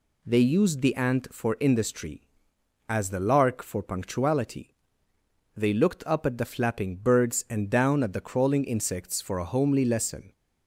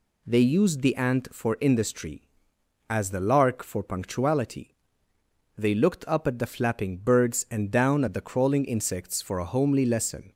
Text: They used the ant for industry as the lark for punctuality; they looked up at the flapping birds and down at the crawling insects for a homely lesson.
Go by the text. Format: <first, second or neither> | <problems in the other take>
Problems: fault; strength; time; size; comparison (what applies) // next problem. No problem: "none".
neither | none